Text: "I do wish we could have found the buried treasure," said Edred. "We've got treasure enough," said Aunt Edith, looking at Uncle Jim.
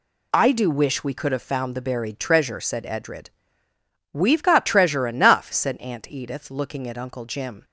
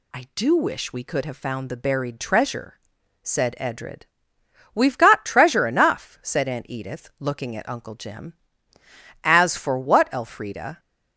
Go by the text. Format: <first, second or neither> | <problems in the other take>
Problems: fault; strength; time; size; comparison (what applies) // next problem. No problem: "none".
first | goes on to say "As for what Elfrida"; from 9.2 s on; 1.5 s long